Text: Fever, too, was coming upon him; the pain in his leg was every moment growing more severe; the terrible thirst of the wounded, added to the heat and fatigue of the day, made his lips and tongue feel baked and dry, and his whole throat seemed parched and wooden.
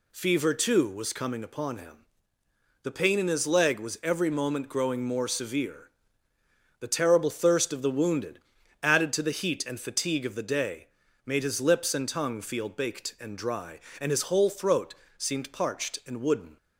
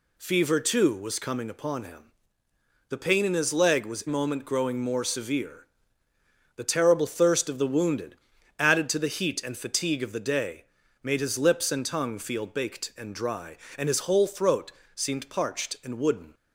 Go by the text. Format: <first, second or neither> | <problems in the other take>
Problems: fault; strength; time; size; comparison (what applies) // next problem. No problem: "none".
first | skips "every"; at 4.0 s // pauses between "throat" and "seemed"; slight; at 14.7 s; 0.22 s long; slight in the first